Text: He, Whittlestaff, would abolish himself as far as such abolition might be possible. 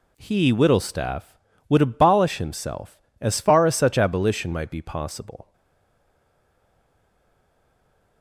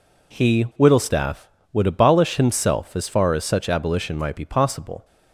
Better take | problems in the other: second | stays silent after the last word; strong; from 5.5 s on; 2.7 s long

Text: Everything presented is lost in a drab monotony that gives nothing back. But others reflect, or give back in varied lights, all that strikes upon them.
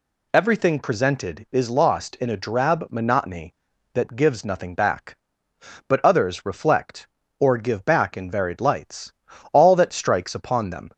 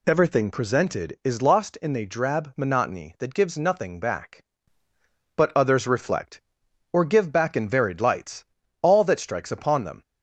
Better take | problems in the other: neither | none

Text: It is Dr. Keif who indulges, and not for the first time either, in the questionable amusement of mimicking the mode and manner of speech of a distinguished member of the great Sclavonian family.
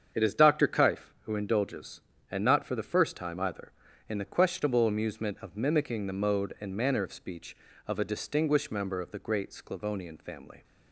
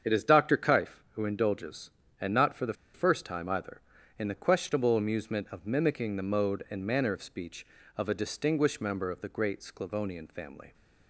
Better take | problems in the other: first | starts louder than the rest; strong; until 1.1 s; 7.5 dB; strong in the first // pauses between "the" and "first"; slight; at 2.7 s; 0.21 s long

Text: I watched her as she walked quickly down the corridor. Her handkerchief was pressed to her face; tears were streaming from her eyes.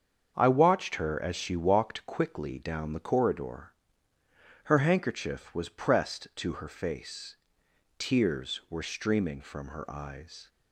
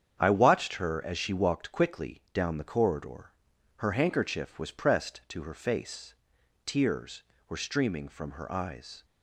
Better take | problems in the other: neither | starts louder than the rest; strong; the same in both

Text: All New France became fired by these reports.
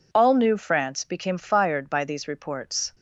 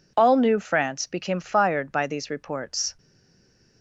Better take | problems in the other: first | stays silent after the last word; slight; from 2.9 s on; 0.9 s long

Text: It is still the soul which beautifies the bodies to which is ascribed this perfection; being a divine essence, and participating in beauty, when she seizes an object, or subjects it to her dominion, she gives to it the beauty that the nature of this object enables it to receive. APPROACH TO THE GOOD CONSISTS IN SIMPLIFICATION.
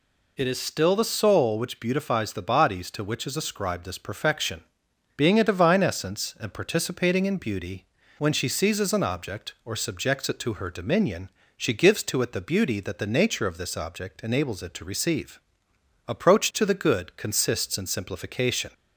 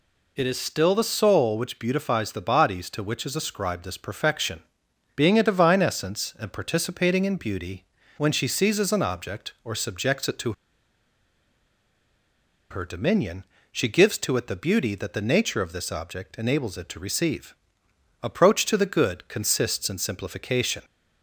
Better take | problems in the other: first | pauses between "to" and "her"; strong; at 10.5 s; 2.1 s long

